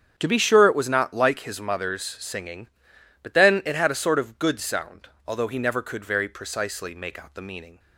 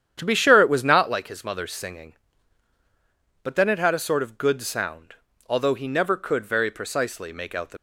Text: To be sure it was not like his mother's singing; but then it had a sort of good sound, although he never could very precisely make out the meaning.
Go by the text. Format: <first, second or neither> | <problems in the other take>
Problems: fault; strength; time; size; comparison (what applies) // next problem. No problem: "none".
first | starts louder than the rest; strong; until 1.1 s; 9.5 dB; strong in the first // stops before "meaning"; at 7.7 s